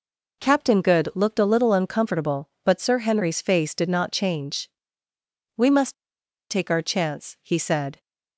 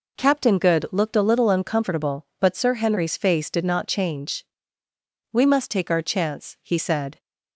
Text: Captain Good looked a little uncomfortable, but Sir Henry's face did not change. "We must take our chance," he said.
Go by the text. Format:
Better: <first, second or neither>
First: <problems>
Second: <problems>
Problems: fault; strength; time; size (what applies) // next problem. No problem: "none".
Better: second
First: pauses between "must" and "take"; noticeable; at 5.9 s; 0.55 s long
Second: none